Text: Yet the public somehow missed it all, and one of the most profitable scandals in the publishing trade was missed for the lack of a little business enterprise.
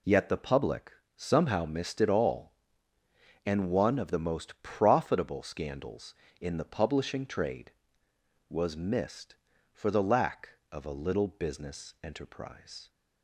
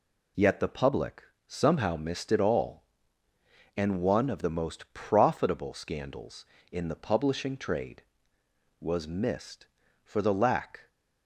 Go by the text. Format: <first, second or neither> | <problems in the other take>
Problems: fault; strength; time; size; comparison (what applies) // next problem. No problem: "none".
first | pauses between "public" and "somehow"; slight; at 1.2 s; 0.24 s long; slight in the first // stops before "of a little business enterprise"; at 10.8 s